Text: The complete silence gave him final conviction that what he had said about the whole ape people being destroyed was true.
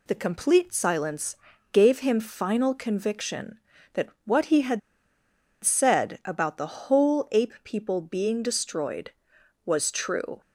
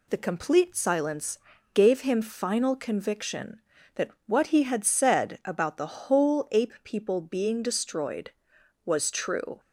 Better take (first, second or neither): second